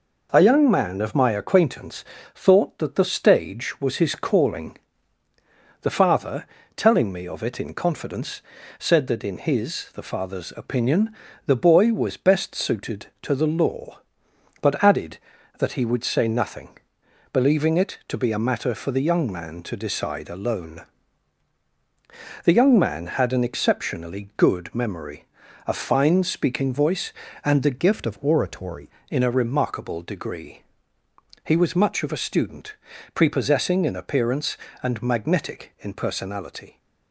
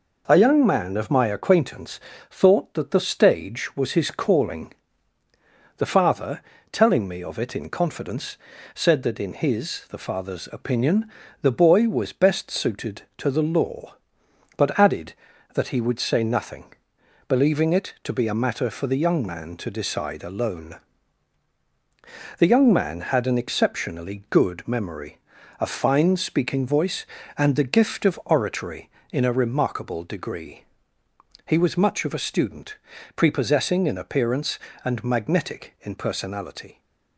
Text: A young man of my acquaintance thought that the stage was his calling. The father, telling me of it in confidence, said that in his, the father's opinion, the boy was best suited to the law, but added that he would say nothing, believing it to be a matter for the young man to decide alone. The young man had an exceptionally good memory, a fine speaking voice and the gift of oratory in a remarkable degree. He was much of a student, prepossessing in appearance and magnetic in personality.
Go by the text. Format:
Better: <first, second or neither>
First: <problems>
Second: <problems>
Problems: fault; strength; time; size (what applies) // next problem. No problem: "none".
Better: second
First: pauses between "acquaintance" and "thought"; slight; at 2.0 s; 0.32 s long // changes voice from "gift" to "oratory"; from 27.7 to 28.8 s; 1.1 s long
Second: pauses between "acquaintance" and "thought"; slight; at 2.0 s; 0.32 s long